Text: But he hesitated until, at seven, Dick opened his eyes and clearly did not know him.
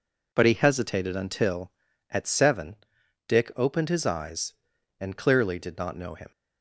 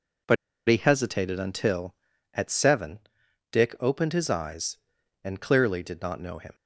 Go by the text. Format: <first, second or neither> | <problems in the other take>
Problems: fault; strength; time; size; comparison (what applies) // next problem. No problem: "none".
first | pauses between "But" and "he"; slight; at 0.3 s; 0.32 s long